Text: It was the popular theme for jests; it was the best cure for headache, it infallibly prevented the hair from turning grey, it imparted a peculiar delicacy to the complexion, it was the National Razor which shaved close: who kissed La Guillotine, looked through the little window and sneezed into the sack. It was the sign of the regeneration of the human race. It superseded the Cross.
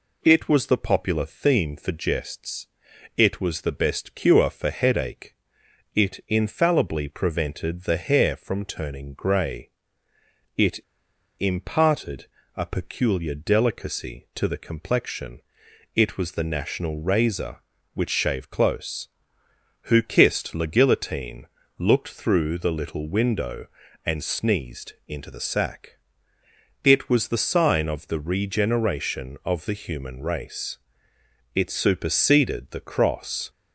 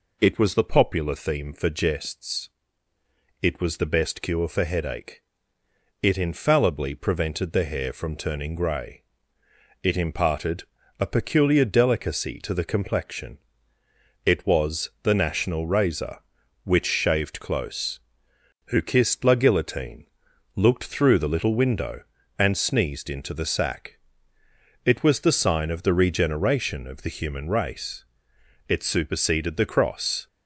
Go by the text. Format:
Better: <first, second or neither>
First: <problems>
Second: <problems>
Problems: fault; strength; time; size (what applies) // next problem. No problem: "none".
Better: second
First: pauses between "it" and "imparted"; noticeable; at 10.7 s; 0.61 s long // pauses between "imparted" and "a"; slight; at 12.2 s; 0.30 s long // pauses between "sneezed" and "into"; slight; at 24.9 s; 0.16 s long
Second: pauses between "imparted" and "a"; slight; at 10.6 s; 0.34 s long